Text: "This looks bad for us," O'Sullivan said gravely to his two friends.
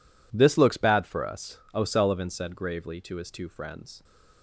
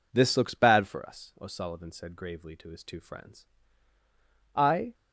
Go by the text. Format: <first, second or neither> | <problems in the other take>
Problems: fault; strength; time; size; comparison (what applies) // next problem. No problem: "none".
first | goes on to say "I"; slight; from 4.5 s on; 0.40 s long